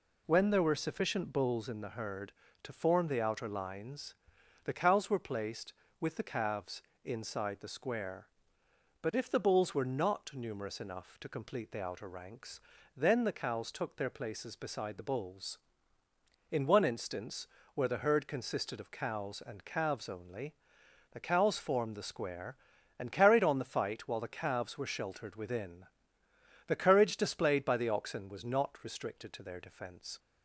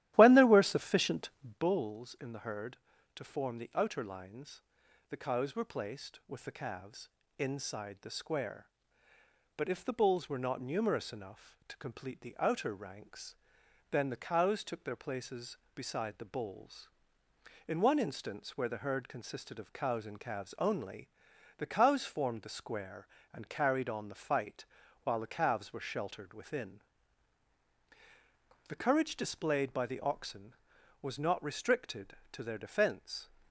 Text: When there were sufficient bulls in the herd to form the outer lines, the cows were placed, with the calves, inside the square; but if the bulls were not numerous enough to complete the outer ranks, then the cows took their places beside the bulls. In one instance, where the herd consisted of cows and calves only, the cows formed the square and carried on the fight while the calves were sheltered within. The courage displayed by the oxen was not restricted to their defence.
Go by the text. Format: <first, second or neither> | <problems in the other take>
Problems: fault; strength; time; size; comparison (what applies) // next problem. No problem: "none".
first | starts louder than the rest; strong; until 1.7 s; 14 dB // pauses between "sufficient" and "bulls"; slight; at 1.2 s; 0.30 s long // pauses between "fight" and "while"; at 24.6 s; 0.40 s long